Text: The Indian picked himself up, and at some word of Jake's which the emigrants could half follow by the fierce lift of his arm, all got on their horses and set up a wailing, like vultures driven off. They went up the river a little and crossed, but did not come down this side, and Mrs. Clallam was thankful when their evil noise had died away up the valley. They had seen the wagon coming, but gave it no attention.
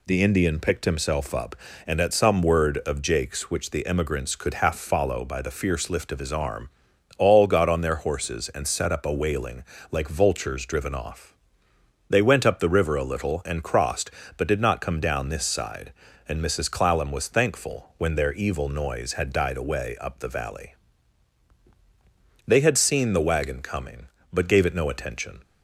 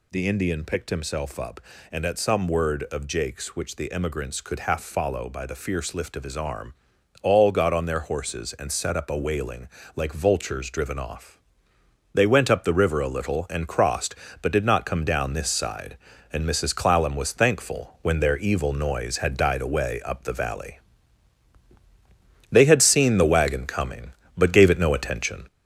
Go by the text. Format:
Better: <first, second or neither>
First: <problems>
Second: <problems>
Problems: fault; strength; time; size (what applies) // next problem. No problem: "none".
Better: first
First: none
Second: gets louder; noticeable; throughout; 5 dB